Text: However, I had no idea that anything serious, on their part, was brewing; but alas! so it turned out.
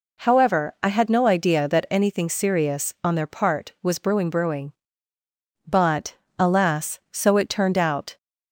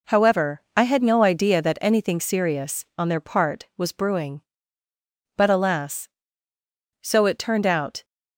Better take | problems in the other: second | says "brewing" twice; at 4.3 s // pauses between "but" and "alas"; slight; at 6.1 s; 0.24 s long

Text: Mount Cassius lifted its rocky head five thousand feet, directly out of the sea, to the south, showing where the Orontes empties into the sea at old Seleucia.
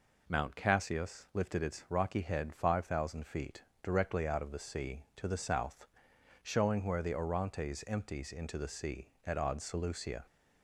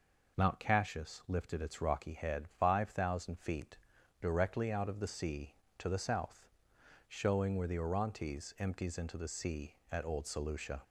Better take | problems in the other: second | says "odd" for "old"; at 9.3 s

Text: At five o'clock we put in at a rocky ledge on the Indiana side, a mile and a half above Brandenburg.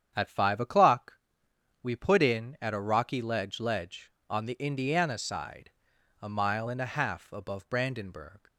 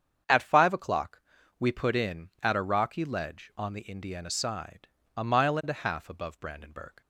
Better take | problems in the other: second | starts louder than the rest; strong; until 1.8 s; 8.5 dB; strong in the second // pauses between "o'clock" and "we"; noticeable; at 1.1 s; 0.68 s long; also in the second // says "ledge" twice; at 3.5 s

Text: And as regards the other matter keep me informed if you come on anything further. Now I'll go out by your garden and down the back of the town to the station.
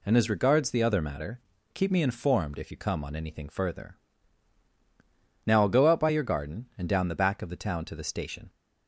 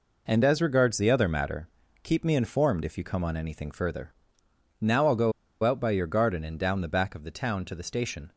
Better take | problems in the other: first | pauses between "matter" and "keep"; slight; at 1.6 s; 0.34 s long; slight in the first // pauses between "go" and "out"; slight; at 5.3 s; 0.31 s long

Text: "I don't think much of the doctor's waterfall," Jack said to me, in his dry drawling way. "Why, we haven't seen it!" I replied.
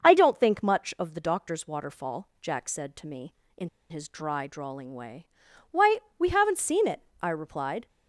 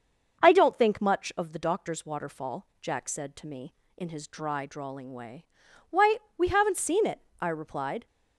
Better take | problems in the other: second | starts louder than the rest; until 1.0 s; 6.5 dB; also in the second // pauses between "in" and "his"; slight; at 3.6 s; 0.21 s long

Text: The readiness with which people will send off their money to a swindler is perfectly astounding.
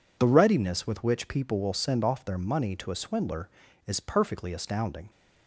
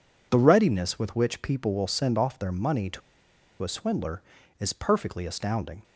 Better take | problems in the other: first | pauses between "to" and "a"; noticeable; at 3.0 s; 0.62 s long

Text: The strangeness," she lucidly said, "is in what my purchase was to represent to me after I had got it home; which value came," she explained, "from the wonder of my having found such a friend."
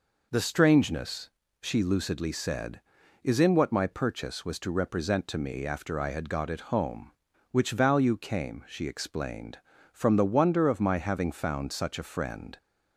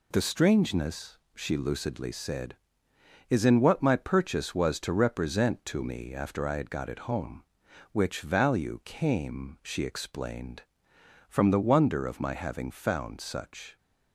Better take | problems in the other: first | stops before "a friend"; at 13.7 s

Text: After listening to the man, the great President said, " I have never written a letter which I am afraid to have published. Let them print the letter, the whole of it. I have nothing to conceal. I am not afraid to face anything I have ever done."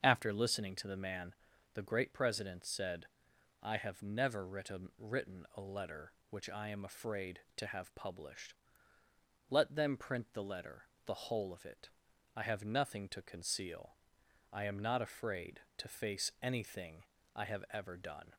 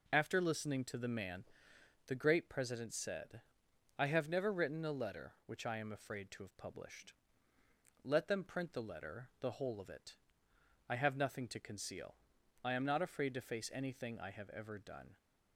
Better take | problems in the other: second | starts louder than the rest; until 1.0 s; 7 dB // says "written" twice; at 4.9 s // pauses between "anything" and "I"; slight; at 17.0 s; 0.32 s long

